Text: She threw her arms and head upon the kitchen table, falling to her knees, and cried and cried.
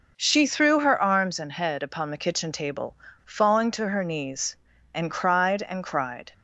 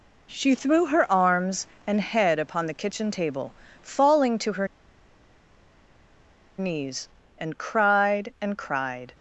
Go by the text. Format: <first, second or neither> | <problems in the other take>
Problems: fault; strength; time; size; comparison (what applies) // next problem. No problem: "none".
first | pauses between "her" and "knees"; strong; at 4.6 s; 1.9 s long